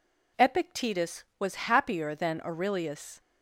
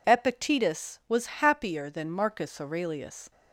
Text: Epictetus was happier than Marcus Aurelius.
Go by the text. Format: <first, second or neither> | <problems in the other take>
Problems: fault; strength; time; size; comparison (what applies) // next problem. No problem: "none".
second | skips "Marcus"; at 2.4 s